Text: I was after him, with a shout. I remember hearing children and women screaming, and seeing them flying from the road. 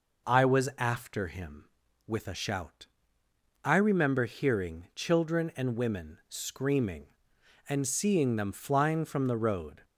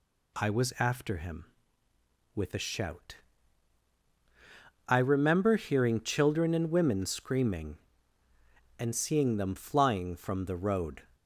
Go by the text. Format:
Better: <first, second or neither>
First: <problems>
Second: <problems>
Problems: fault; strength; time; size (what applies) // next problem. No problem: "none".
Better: neither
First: none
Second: none